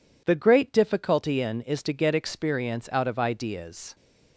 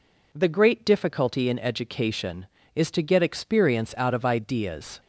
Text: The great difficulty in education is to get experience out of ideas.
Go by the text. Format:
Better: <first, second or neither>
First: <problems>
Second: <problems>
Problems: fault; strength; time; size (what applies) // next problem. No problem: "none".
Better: second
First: skips "education"; at 1.6 s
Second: none